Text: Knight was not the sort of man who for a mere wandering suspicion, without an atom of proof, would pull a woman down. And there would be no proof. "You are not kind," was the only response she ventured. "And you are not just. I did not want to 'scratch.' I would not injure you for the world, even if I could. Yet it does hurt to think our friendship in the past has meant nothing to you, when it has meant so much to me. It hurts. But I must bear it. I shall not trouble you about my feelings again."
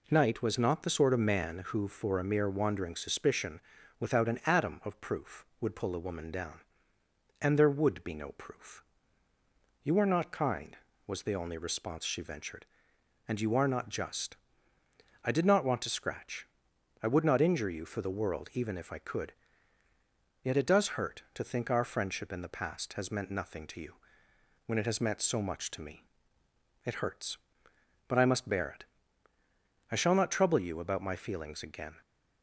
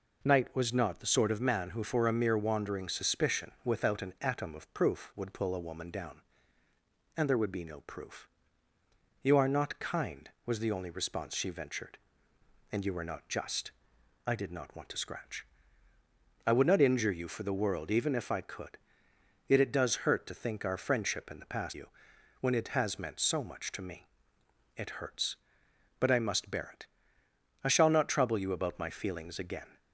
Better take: first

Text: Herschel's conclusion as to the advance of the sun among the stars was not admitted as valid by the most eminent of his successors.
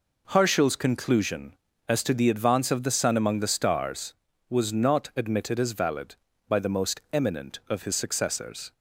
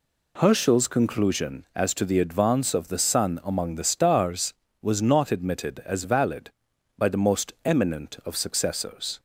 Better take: first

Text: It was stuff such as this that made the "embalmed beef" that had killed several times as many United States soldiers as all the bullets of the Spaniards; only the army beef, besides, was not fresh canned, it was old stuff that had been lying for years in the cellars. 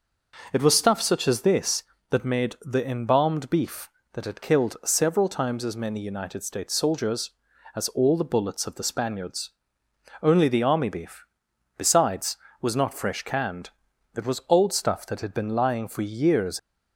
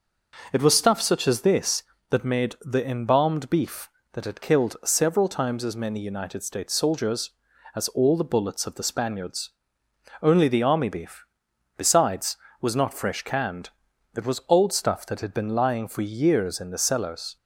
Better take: second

